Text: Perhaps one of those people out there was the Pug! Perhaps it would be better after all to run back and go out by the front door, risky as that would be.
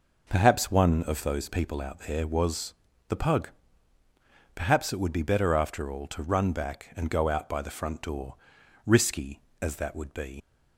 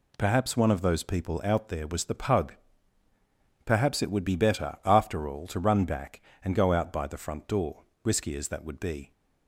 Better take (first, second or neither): second